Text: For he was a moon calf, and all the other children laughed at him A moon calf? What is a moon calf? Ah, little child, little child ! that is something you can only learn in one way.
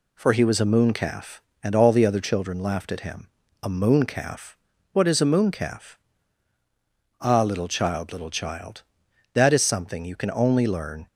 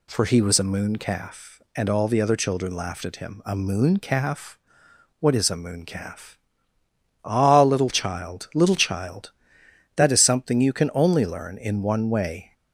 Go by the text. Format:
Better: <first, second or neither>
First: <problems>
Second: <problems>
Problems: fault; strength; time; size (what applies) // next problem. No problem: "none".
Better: second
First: pauses between "him" and "A"; slight; at 3.2 s; 0.34 s long // stops before "in one way"; at 11.0 s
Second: none